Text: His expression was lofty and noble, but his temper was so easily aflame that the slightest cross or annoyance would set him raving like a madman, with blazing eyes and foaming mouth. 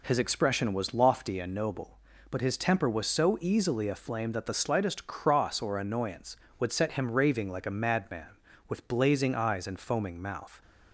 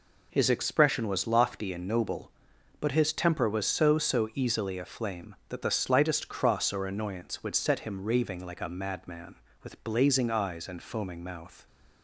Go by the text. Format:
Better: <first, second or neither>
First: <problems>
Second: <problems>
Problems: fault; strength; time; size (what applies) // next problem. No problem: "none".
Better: first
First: none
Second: says "so" twice; at 3.9 s